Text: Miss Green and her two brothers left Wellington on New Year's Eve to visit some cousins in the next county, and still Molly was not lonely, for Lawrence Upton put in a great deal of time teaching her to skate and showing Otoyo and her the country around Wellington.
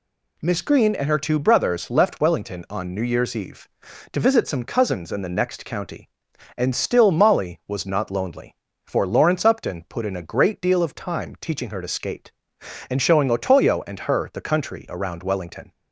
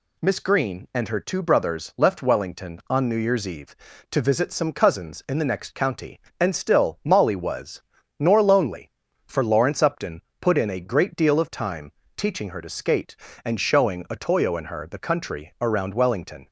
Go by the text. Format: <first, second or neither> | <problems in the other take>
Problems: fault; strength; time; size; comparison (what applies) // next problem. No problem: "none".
first | says "nor" for "not"; at 8.1 s // pauses between "Upton" and "put"; slight; at 10.2 s; 0.18 s long // pauses between "time" and "teaching"; slight; at 11.9 s; 0.24 s long